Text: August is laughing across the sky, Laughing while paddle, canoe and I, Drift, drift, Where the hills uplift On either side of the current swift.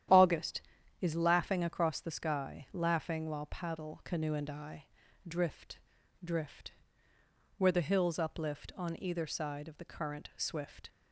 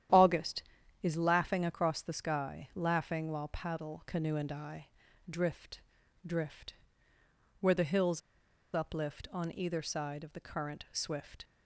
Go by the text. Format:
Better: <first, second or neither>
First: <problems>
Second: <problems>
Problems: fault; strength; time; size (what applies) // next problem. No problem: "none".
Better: first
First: starts louder than the rest; strong; until 1.5 s; 10.5 dB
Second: starts louder than the rest; strong; until 1.5 s; 10.5 dB // pauses between "hills" and "uplift"; noticeable; at 8.2 s; 0.53 s long